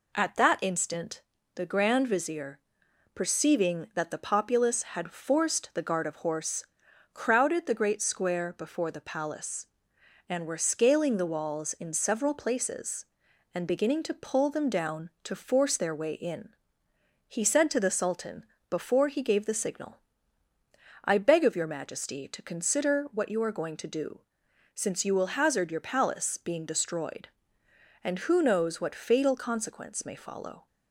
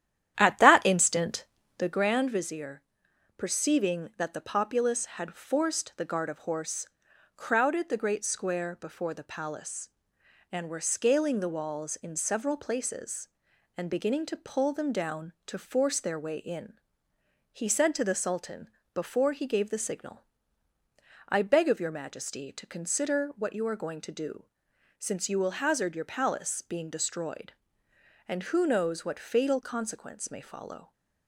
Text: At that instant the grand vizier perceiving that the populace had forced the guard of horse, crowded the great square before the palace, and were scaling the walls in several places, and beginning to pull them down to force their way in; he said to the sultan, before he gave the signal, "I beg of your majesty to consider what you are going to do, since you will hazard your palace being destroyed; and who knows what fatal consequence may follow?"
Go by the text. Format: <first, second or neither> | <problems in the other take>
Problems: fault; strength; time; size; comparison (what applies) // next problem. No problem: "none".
first | starts louder than the rest; strong; until 2.1 s; 11 dB // pauses between "instant" and "the"; slight; at 1.4 s; 0.32 s long; slight in the first // pauses between "vizier" and "perceiving"; noticeable; at 2.8 s; 0.54 s long; noticeable in the first